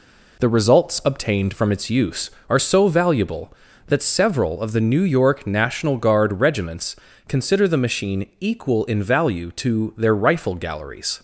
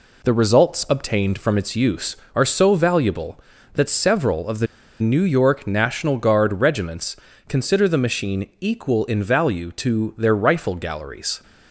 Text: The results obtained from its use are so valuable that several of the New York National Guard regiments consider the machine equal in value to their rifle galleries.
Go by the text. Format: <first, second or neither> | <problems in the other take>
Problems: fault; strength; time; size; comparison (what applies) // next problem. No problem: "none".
first | pauses between "the" and "New"; slight; at 4.6 s; 0.33 s long // pauses between "regiments" and "consider"; slight; at 7.1 s; 0.32 s long; slight in the first